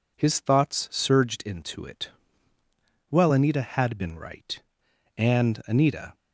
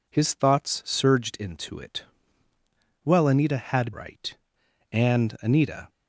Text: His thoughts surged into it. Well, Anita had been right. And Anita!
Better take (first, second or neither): first